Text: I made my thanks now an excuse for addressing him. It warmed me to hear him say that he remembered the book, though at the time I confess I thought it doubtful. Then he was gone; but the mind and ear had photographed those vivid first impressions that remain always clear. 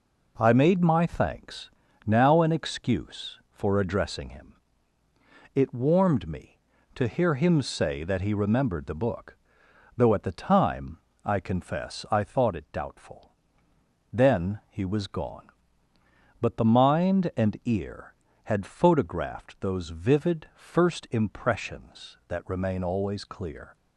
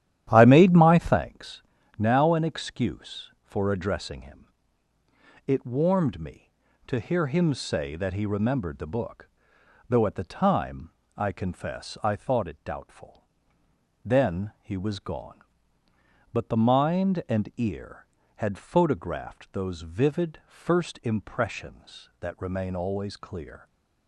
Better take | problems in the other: first | starts louder than the rest; strong; until 1.2 s; 11.5 dB // pauses between "thanks" and "now"; slight; at 1.6 s; 0.36 s long; slight in the first // pauses between "time" and "I"; slight; at 10.9 s; 0.26 s long; slight in the first

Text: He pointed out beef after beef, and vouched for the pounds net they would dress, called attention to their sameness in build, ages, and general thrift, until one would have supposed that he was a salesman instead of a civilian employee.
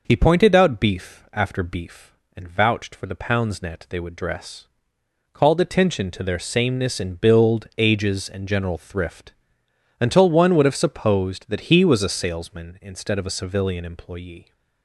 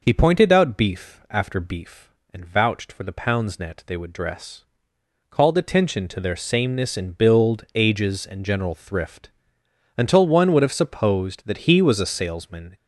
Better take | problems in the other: first | stops before "instead of a civilian employee"; at 12.7 s

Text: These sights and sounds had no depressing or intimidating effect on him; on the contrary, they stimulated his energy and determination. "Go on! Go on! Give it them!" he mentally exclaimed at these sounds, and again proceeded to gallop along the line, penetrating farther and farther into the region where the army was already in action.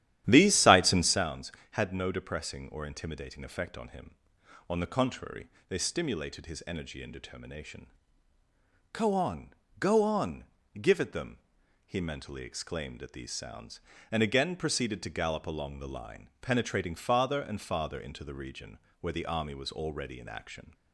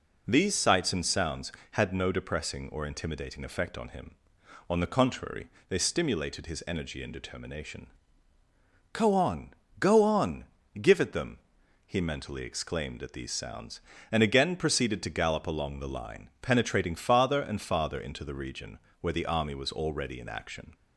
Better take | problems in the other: second | starts louder than the rest; strong; until 1.3 s; 11.5 dB // pauses between "region" and "where"; slight; at 18.7 s; 0.22 s long; slight in the second

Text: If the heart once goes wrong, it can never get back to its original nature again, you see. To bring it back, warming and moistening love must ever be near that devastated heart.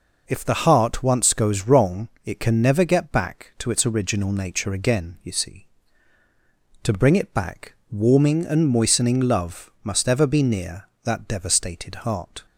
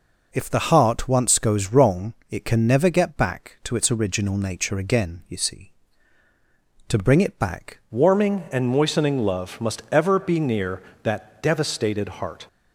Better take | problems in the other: first | changes voice at "warming"; from 7.9 s on; 4.5 s long

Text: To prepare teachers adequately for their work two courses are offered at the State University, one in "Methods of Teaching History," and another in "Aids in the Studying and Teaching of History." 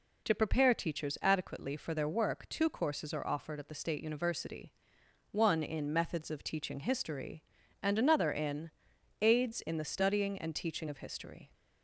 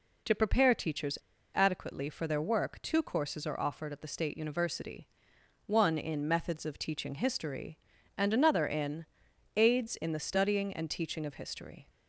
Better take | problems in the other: first | pauses between "teachers" and "adequately"; at 1.1 s; 0.38 s long // pauses between "in" and "Aids"; noticeable; at 9.0 s; 0.50 s long; noticeable in the first

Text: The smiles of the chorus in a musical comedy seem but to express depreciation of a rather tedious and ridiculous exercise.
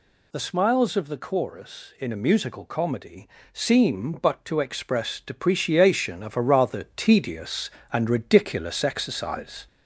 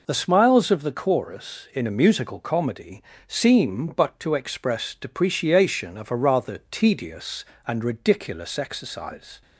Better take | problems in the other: second | gets louder; slight; throughout; 2.5 dB // pauses between "comedy" and "seem"; slight; at 3.2 s; 0.24 s long; slight in the second

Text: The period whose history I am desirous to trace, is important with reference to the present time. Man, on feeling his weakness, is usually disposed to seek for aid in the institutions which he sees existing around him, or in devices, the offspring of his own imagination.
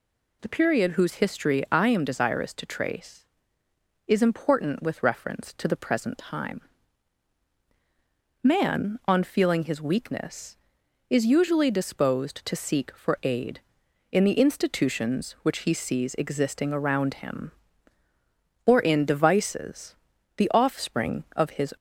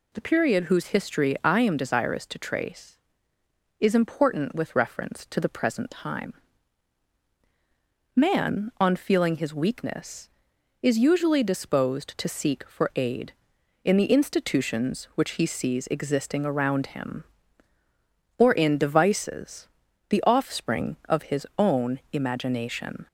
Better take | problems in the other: second | stops before "own imagination"; at 21.7 s

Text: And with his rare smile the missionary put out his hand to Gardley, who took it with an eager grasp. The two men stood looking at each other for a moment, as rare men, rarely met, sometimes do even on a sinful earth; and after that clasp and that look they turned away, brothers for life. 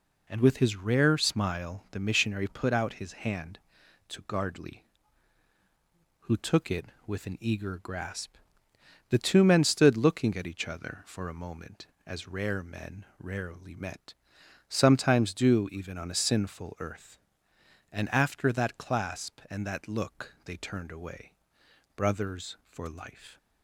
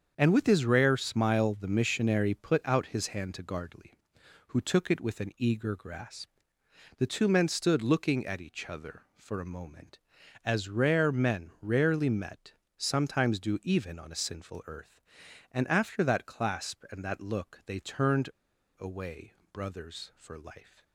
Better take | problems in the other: first | starts louder than the rest; strong; until 1.1 s; 7 dB // pauses between "turned" and "away"; noticeable; at 18.2 s; 0.50 s long

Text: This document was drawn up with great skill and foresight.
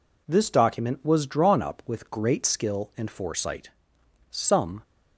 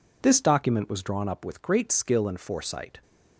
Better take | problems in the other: second | goes on to say "Some"; from 4.3 s on; 0.50 s long

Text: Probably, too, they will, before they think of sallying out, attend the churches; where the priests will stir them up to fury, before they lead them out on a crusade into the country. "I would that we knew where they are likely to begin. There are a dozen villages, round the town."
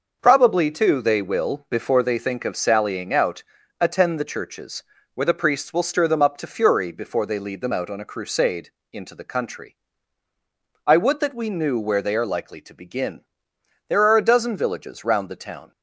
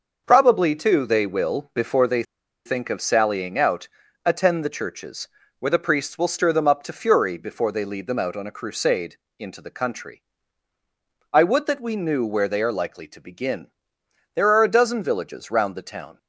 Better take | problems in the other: first | starts louder than the rest; until 1.2 s; 6 dB; also in the first // pauses between "they" and "think"; at 2.2 s; 0.42 s long // pauses between "crusade" and "into"; slight; at 9.1 s; 0.22 s long; slight in the first

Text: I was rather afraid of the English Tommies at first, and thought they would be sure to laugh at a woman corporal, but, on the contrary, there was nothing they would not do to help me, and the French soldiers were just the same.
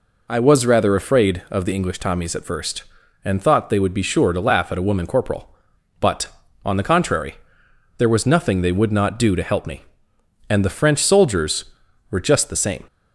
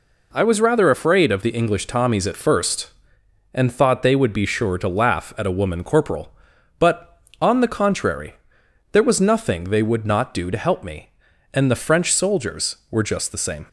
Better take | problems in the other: neither | none

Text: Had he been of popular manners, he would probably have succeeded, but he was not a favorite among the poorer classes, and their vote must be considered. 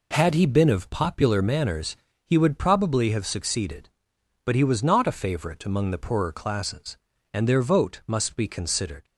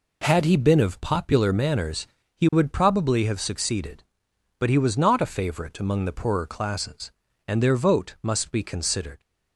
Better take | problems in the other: neither | none

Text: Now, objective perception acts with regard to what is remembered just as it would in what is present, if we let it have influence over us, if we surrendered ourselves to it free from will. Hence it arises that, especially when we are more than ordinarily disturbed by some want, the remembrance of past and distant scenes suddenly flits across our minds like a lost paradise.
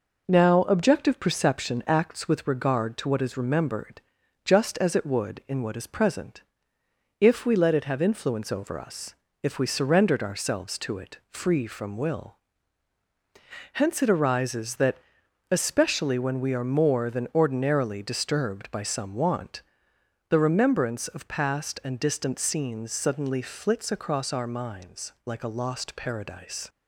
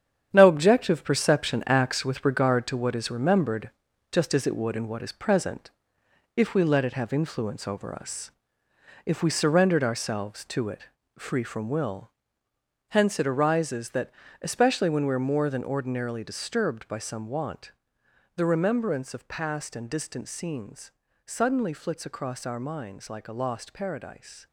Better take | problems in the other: first | gets quieter; strong; throughout; 9 dB // pauses between "remembered" and "just"; at 3.7 s; 0.40 s long; also in the first // pauses between "it" and "free"; slight; at 10.8 s; 0.36 s long // pauses between "scenes" and "suddenly"; slight; at 20.9 s; 0.36 s long

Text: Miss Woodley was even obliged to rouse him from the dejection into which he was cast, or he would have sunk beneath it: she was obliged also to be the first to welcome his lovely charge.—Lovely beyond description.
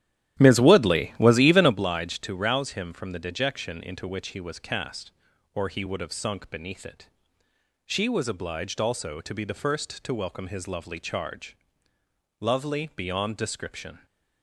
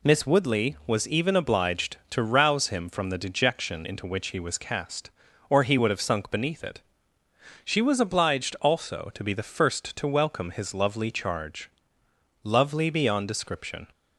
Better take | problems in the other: second | starts louder than the rest; strong; until 1.8 s; 12 dB

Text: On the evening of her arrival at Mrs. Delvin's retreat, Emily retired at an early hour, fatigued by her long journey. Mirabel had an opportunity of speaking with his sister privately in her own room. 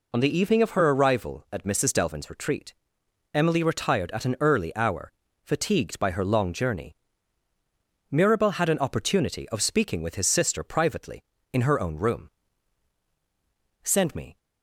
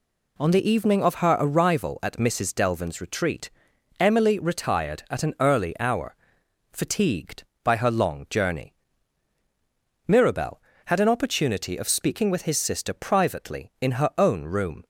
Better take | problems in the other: second | goes on to say "Send me"; from 13.8 s on; 0.56 s long

